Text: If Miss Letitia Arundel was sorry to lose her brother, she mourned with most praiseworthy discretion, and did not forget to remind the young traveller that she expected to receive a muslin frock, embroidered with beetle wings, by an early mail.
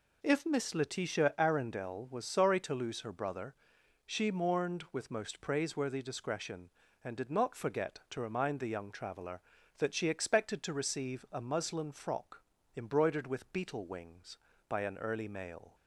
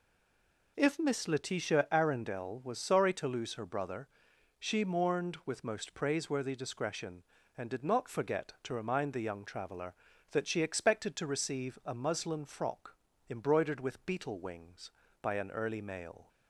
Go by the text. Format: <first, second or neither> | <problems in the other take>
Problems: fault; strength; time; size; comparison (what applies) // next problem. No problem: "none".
first | stays silent before the first word; slight; until 0.7 s; 0.7 s long